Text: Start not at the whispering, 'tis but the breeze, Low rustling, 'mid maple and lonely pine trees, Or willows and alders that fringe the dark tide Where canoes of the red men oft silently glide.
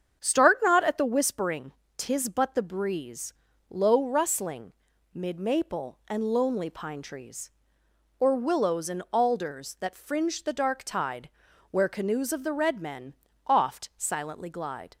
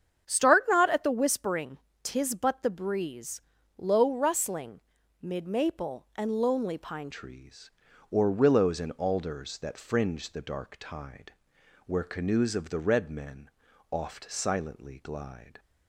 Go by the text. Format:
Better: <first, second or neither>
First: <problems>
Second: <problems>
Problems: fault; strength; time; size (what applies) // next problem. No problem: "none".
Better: first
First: starts louder than the rest; strong; until 1.2 s; 8 dB // pauses between "tide" and "Where"; at 11.2 s; 0.40 s long // pauses between "men" and "oft"; slight; at 13.1 s; 0.34 s long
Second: starts louder than the rest; strong; until 1.2 s; 8 dB // changes voice at "trees"; from 7.1 s on; 8.4 s long // pauses between "tide" and "Where"; noticeable; at 11.3 s; 0.52 s long // pauses between "men" and "oft"; at 13.4 s; 0.42 s long